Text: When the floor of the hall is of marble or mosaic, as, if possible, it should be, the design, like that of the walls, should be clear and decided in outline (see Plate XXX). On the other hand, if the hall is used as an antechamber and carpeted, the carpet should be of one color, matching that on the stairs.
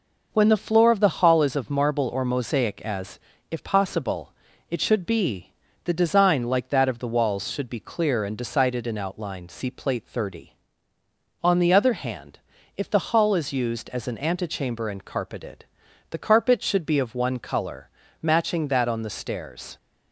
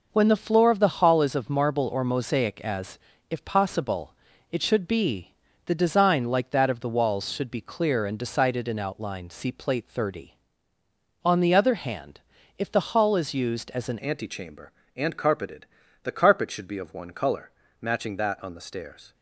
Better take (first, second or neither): first